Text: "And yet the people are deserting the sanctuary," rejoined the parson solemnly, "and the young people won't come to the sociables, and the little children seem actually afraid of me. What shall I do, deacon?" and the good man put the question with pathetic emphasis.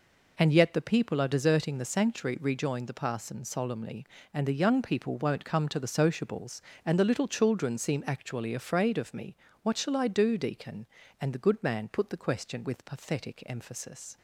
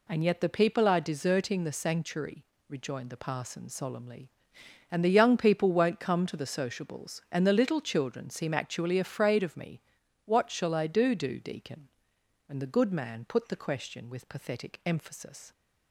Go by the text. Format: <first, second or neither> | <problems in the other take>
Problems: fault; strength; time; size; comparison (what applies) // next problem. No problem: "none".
first | says "do" twice; at 11.1 s